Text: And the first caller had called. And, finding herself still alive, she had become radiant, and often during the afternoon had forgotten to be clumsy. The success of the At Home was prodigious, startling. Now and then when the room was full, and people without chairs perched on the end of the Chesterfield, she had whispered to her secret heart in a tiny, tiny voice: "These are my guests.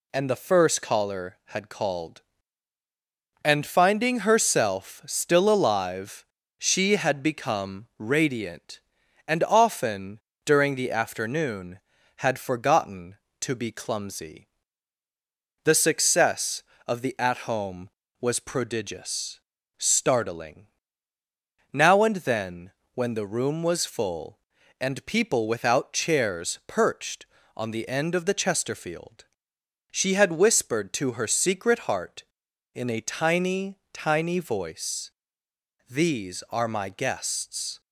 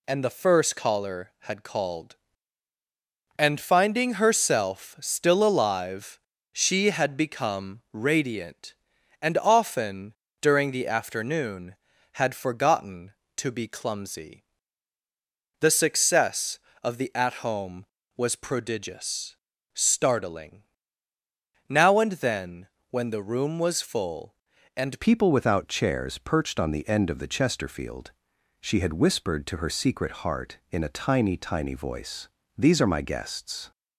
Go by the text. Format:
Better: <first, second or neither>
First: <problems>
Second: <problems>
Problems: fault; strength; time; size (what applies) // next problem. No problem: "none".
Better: first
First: pauses between "often" and "during"; slight; at 10.1 s; 0.26 s long // pauses between "then" and "when"; slight; at 22.7 s; 0.22 s long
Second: pauses between "often" and "during"; slight; at 10.1 s; 0.28 s long // pauses between "then" and "when"; slight; at 22.6 s; 0.22 s long // changes voice at "people"; from 25.0 s on; 8.7 s long